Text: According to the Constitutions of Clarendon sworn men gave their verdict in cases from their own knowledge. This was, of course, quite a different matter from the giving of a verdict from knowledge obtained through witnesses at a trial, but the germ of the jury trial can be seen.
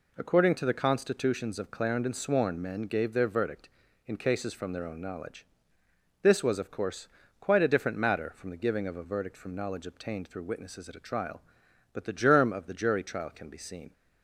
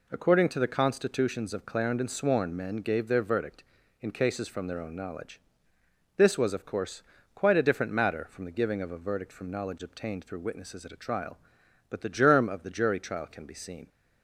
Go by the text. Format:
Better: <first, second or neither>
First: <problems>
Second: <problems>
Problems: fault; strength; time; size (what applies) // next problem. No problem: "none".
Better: neither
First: none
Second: none